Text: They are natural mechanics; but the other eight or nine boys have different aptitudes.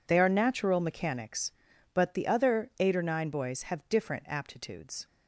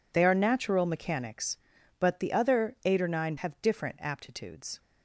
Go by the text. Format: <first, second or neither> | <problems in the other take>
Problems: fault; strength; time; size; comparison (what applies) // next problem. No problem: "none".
first | skips "boys"; at 3.3 s